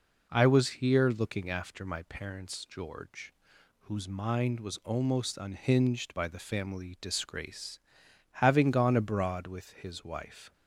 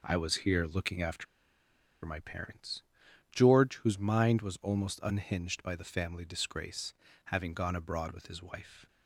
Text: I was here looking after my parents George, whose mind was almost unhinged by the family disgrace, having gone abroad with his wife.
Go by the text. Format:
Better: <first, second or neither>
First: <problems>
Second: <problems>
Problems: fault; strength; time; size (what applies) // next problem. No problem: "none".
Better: first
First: none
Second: pauses between "after" and "my"; noticeable; at 1.2 s; 0.80 s long // pauses between "parents" and "George"; noticeable; at 2.8 s; 0.48 s long